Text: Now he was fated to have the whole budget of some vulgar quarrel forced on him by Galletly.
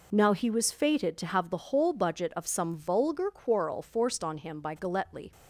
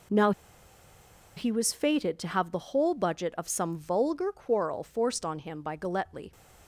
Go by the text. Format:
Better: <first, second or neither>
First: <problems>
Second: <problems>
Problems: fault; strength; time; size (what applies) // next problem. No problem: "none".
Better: first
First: none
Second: pauses between "Now" and "he"; at 0.3 s; 1.0 s long